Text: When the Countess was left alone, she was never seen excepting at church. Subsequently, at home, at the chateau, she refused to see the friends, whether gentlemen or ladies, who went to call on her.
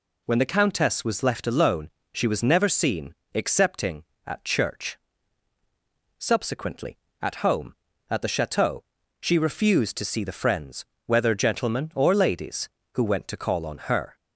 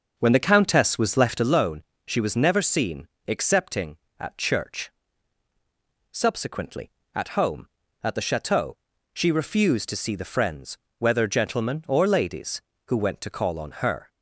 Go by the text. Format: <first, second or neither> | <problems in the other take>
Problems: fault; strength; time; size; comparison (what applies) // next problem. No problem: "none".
first | starts louder than the rest; noticeable; until 1.5 s; 6 dB // pauses between "seen" and "excepting"; slight; at 3.0 s; 0.18 s long; slight in the first